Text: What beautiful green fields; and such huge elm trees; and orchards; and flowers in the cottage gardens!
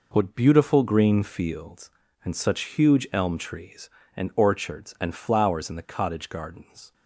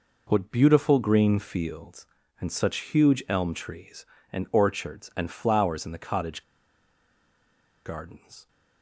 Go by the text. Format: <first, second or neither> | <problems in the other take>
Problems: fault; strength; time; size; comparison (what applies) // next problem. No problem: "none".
first | pauses between "cottage" and "gardens"; strong; at 6.4 s; 1.4 s long